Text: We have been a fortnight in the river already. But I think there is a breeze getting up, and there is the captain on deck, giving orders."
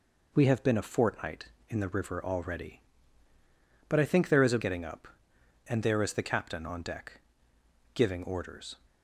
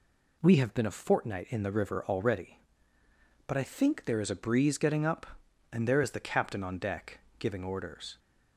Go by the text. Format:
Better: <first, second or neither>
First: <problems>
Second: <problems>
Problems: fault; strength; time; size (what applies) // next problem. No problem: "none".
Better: second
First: skips "breeze"; at 4.5 s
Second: none